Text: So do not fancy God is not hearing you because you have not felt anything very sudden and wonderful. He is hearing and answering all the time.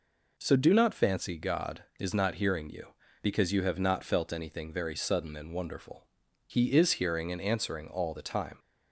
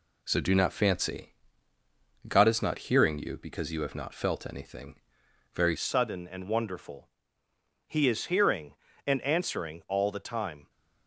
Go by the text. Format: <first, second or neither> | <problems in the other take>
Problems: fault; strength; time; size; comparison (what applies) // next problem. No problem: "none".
first | pauses between "fancy" and "God"; at 1.2 s; 1.0 s long // pauses between "anything" and "very"; noticeable; at 4.9 s; 0.62 s long // changes voice at "sudden"; from 5.7 s on; 4.9 s long